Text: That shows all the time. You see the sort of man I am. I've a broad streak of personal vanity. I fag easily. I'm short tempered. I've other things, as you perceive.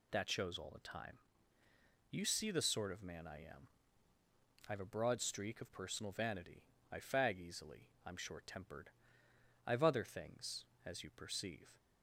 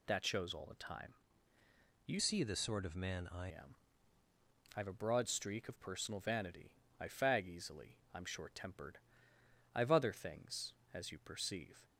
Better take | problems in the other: first | changes voice from "see" to "I"; from 2.1 to 3.4 s; 1.3 s long

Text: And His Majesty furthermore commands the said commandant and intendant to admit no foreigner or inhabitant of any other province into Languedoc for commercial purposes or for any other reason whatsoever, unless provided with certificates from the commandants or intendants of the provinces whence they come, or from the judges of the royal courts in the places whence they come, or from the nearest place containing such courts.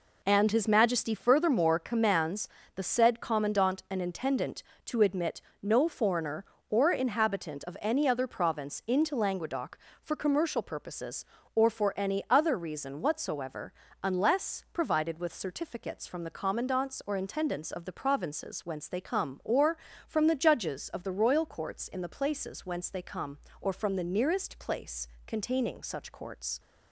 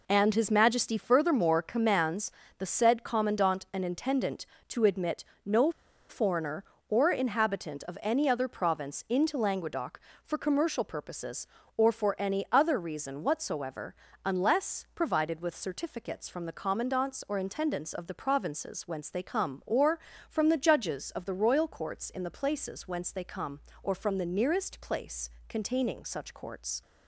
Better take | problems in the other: first | pauses between "commands" and "the"; slight; at 2.3 s; 0.28 s long; slight in the first // pauses between "admit" and "no"; slight; at 5.2 s; 0.20 s long; slight in the first // pauses between "no" and "foreigner"; at 5.7 s; 0.38 s long // pauses between "place" and "containing"; slight; at 25.2 s; 0.18 s long; slight in the first

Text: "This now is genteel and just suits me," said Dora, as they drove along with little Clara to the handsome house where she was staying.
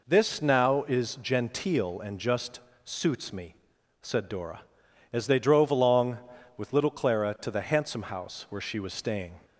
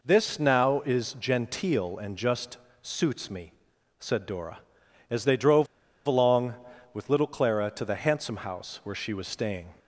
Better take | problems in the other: first | pauses between "just" and "suits"; slight; at 2.5 s; 0.24 s long; slight in the first // pauses between "drove" and "along"; at 5.6 s; 0.41 s long

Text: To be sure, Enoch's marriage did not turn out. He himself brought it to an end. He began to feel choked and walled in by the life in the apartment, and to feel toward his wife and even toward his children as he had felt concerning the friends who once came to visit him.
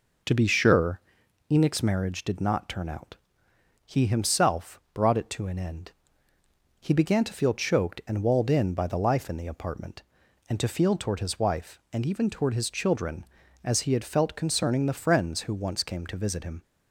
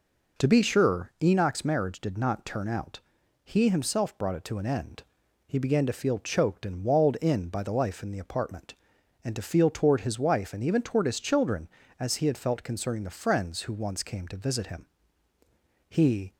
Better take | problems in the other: first | goes on to say "He"; slight; from 15.8 s on; 0.46 s long

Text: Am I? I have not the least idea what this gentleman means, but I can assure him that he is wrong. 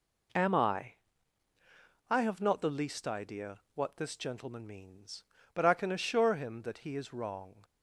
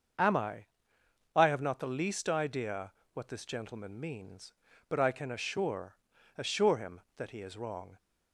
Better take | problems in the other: first | starts louder than the rest; until 1.8 s; 6.5 dB // pauses between "idea" and "what"; slight; at 2.9 s; 0.22 s long; slight in the first // says "assure" twice; at 6.3 s

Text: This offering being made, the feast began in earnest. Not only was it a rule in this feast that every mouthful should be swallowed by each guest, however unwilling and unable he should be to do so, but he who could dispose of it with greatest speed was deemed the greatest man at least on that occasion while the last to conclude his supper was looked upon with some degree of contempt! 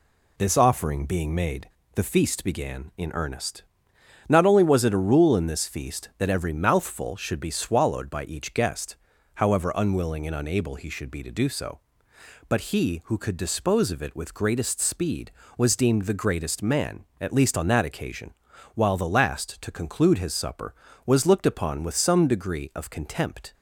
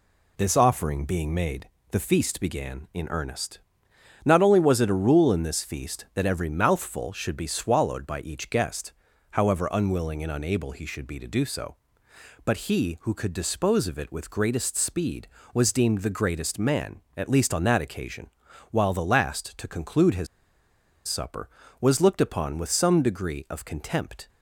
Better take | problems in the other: first | pauses between "occasion" and "while"; at 18.2 s; 0.42 s long; also in the first // pauses between "his" and "supper"; noticeable; at 20.2 s; 0.80 s long

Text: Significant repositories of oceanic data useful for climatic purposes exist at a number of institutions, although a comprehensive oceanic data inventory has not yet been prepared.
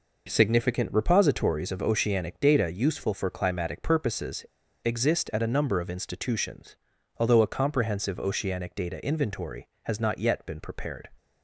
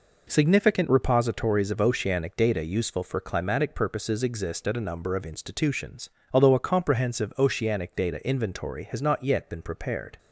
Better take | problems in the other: second | pauses between "purposes" and "exist"; at 4.4 s; 0.40 s long

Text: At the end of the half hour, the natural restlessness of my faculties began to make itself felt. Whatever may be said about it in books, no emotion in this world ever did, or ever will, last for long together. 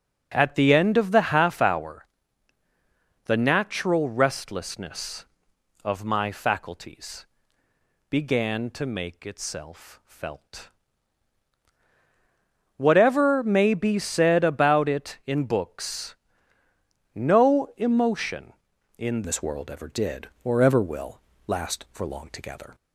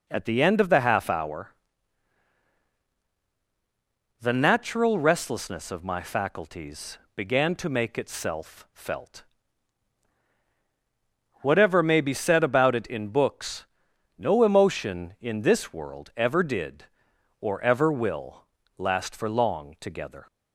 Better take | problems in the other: second | starts louder than the rest; until 1.3 s; 6.5 dB // pauses between "faculties" and "began"; noticeable; at 7.2 s; 0.82 s long; slight in the second // changes voice at "this"; from 19.2 s on; 3.5 s long

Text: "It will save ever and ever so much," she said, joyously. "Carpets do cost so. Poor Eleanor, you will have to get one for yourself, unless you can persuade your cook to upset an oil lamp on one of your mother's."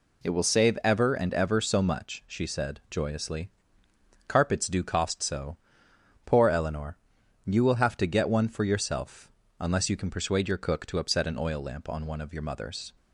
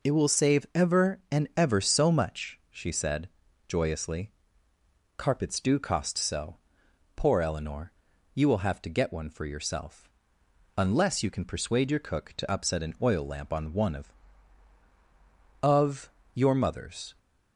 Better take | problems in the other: first | says "of" twice; at 15.6 s

